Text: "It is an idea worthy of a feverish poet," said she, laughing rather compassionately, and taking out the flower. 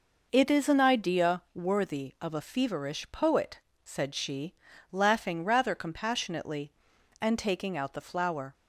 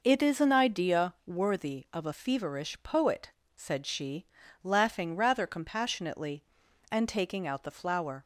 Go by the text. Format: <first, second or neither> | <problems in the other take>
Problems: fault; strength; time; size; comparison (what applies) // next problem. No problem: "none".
neither | none